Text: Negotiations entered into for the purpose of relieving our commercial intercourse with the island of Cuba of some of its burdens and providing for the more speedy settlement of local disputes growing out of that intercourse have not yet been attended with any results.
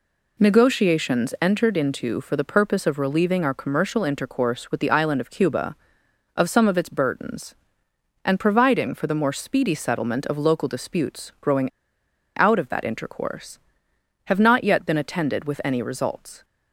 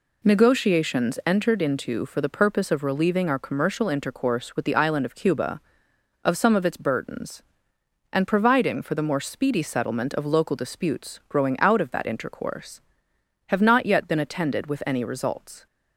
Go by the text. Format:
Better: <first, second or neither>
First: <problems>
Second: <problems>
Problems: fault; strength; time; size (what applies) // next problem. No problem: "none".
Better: second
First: pauses between "growing" and "out"; noticeable; at 11.6 s; 0.69 s long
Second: none